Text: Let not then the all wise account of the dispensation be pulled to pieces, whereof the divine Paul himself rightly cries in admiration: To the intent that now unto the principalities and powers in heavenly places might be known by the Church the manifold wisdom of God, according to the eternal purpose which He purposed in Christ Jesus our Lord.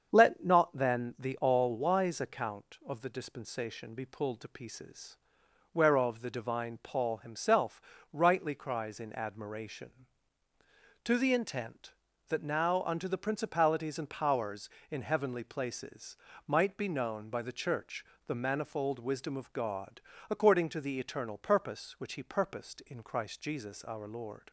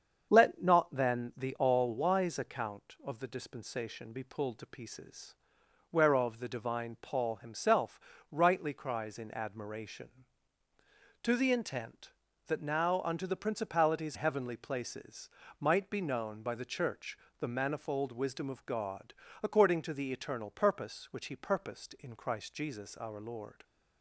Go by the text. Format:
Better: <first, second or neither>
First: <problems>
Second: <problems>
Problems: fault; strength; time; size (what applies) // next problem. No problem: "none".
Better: first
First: starts louder than the rest; strong; until 1.1 s; 7 dB // pauses between "himself" and "rightly"; slight; at 7.7 s; 0.32 s long // pauses between "places" and "might"; slight; at 16.1 s; 0.32 s long // pauses between "Church" and "the"; slight; at 18.0 s; 0.22 s long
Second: starts louder than the rest; strong; until 1.3 s; 7 dB // pauses between "himself" and "rightly"; slight; at 7.9 s; 0.32 s long // skips "and powers in"; at 14.1 s // pauses between "places" and "might"; slight; at 15.2 s; 0.32 s long // pauses between "Church" and "the"; slight; at 17.1 s; 0.22 s long